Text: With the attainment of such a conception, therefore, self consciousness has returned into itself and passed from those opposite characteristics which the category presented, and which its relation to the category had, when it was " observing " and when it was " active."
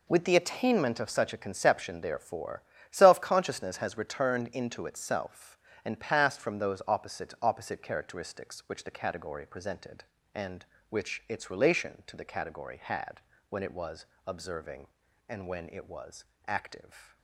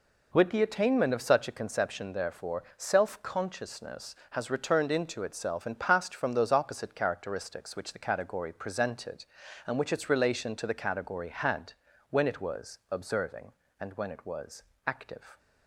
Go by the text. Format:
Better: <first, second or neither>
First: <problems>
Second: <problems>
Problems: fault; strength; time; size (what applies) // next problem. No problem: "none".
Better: second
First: says "opposite" twice; at 7.4 s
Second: none